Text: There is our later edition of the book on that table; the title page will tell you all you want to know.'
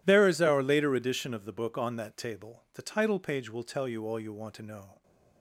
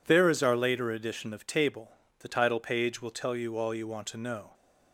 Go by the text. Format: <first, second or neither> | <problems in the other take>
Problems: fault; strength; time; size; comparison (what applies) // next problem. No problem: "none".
first | skips "the book on that"; at 1.4 s